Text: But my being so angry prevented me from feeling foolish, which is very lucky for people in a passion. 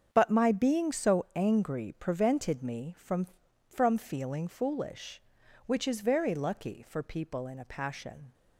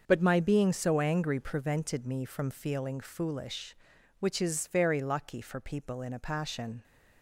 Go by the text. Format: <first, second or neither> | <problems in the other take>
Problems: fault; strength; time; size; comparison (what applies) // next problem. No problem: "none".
second | starts louder than the rest; strong; until 1.1 s; 7.5 dB; also in the second // says "from" twice; at 3.6 s